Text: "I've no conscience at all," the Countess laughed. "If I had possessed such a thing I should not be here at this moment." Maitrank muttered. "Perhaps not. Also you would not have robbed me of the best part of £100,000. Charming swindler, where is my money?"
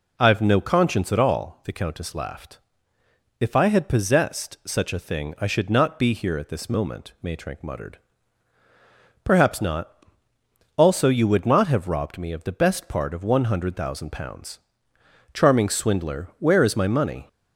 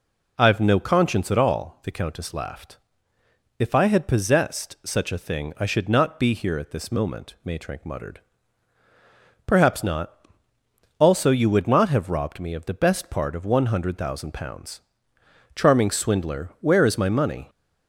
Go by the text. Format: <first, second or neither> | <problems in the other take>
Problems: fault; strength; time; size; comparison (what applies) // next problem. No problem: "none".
neither | none